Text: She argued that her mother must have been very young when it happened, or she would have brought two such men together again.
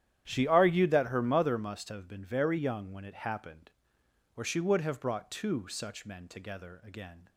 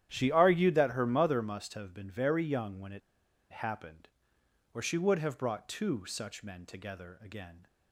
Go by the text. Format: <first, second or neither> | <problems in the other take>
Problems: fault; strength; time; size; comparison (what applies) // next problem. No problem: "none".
first | starts louder than the rest; strong; until 1.1 s; 10.5 dB; strong in the first // pauses between "it" and "happened"; noticeable; at 3.0 s; 0.50 s long